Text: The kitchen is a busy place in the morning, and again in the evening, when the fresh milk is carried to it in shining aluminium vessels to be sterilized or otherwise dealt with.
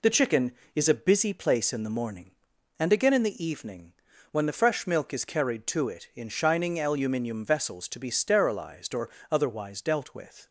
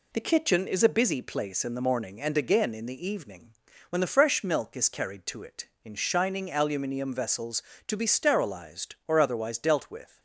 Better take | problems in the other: second | says "chicken" for "kitchen"; at 0.1 s // pauses between "or" and "otherwise"; slight; at 9.0 s; 0.22 s long

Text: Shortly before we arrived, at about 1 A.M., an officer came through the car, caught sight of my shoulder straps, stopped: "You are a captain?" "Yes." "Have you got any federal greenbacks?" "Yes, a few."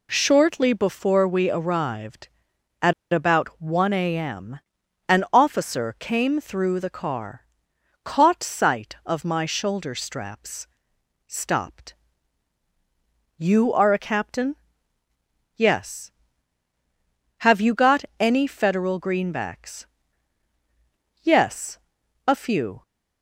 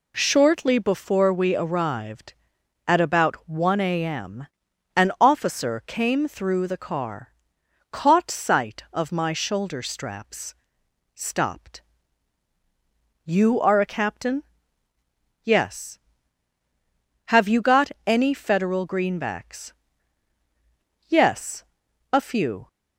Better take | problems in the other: second | pauses between "at" and "about"; slight; at 2.9 s; 0.20 s long // pauses between "got" and "any"; slight; at 18.0 s; 0.16 s long; slight in the second

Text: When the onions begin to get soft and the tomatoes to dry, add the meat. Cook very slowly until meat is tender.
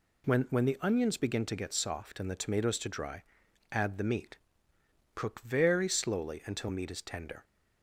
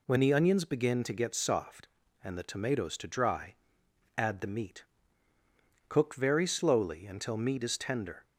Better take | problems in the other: second | says "When" twice; at 0.4 s

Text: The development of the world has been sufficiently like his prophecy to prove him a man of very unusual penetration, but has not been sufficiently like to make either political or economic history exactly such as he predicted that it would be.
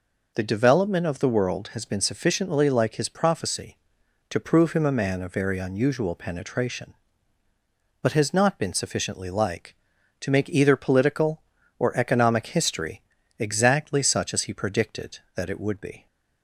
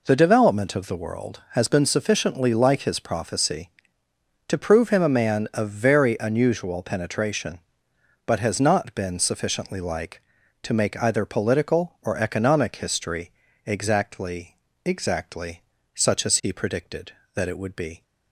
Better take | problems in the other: first | pauses between "history" and "exactly"; slight; at 13.3 s; 0.34 s long; slight in the first // says "exactly" twice; at 14.8 s

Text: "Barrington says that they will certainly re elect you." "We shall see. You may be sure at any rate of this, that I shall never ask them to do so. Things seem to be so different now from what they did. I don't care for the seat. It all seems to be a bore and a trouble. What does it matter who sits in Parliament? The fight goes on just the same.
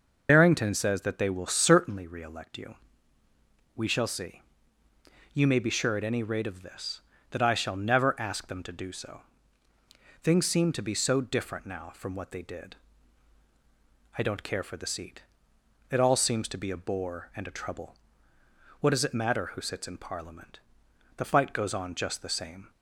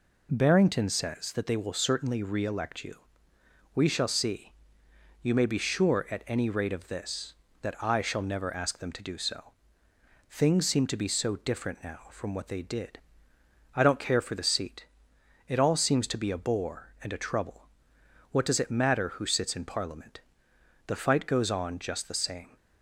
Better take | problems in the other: second | loses the start of "Barrington"; at 0.2 s; 55 ms

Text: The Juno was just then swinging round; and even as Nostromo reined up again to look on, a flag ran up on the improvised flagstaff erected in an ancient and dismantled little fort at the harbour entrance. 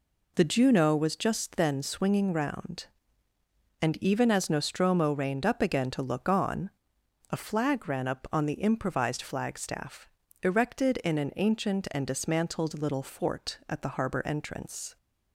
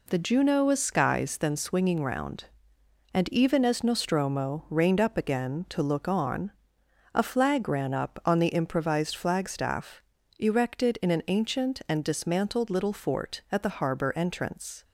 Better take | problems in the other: first | says "skies" for "just"; at 0.8 s // pauses between "flagstaff" and "erected"; slight; at 10.0 s; 0.36 s long; slight in the first

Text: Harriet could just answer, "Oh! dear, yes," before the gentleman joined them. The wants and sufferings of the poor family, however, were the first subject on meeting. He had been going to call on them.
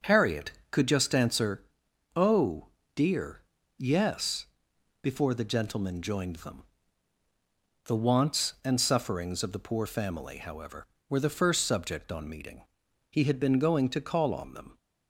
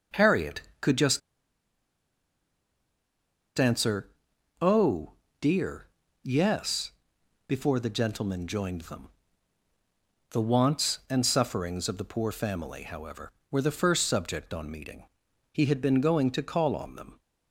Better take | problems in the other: first | starts louder than the rest; until 3.7 s; 6 dB; also in the first // pauses between "just" and "answer"; strong; at 1.2 s; 2.3 s long

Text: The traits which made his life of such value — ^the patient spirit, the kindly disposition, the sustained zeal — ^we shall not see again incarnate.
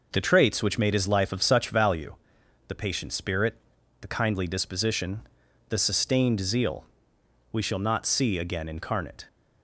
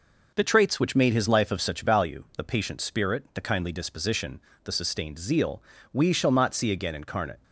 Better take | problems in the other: neither | none

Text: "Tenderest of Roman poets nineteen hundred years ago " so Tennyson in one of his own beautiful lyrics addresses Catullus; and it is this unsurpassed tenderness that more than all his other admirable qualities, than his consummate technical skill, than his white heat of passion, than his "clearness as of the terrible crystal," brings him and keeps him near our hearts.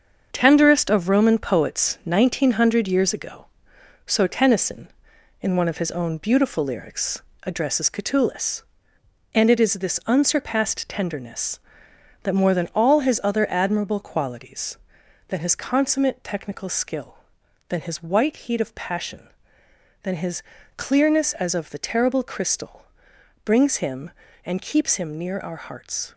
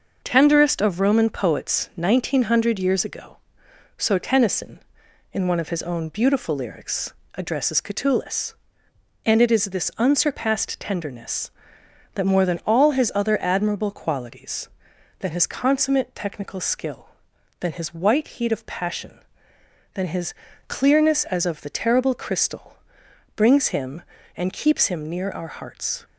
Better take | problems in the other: second | gets quieter; noticeable; throughout; 5.5 dB // starts louder than the rest; until 1.3 s; 7 dB; also in the second // pauses between "lyrics" and "addresses"; slight; at 7.2 s; 0.20 s long; slight in the second // pauses between "his" and "clearness"; slight; at 20.4 s; 0.34 s long; slight in the second

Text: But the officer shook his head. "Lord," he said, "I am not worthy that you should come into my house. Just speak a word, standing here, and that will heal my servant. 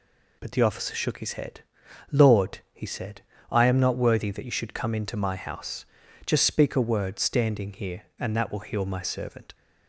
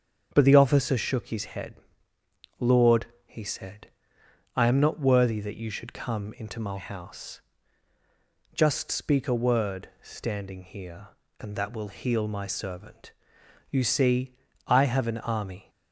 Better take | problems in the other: first | starts louder than the rest; until 1.3 s; 7 dB // goes on to say "You see I have an army"; strong; from 13.6 s on; 2.0 s long

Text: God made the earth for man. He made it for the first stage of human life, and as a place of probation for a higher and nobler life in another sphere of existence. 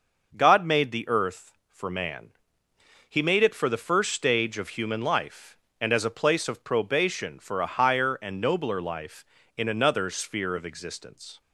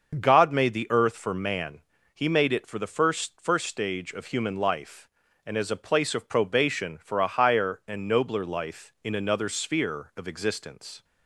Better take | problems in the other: first | starts louder than the rest; until 1.2 s; 6.5 dB // says "first" twice; at 3.3 s

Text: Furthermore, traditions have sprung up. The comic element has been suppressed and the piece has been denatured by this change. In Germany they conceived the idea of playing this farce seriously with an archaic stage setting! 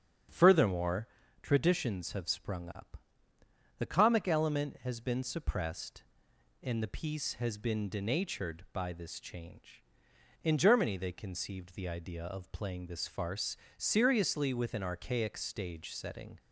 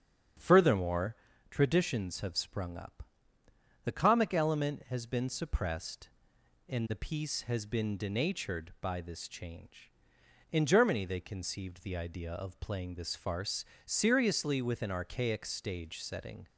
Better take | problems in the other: neither | starts louder than the rest; strong; the same in both // pauses between "farce" and "seriously"; slight; the same in both

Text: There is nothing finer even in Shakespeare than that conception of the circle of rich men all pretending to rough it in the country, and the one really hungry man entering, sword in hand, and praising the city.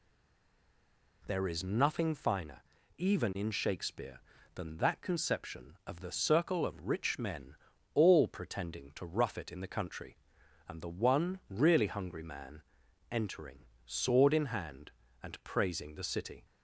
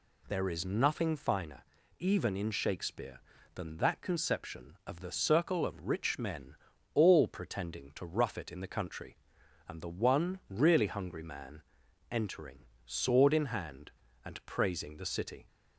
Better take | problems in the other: second | stays silent before the first word; noticeable; until 1.2 s; 1.2 s long // pauses between "finer" and "even"; slight; at 2.6 s; 0.36 s long; slight in the second // pauses between "men" and "all"; at 7.5 s; 0.38 s long; also in the second // pauses between "man" and "entering"; noticeable; at 12.6 s; 0.50 s long; noticeable in the second

